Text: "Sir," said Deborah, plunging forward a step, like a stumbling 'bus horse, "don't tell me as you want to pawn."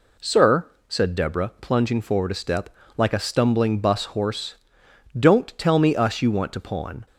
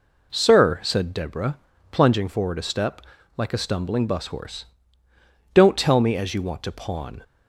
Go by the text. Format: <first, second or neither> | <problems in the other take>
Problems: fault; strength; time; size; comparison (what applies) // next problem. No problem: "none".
second | says "us" for "as"; at 5.9 s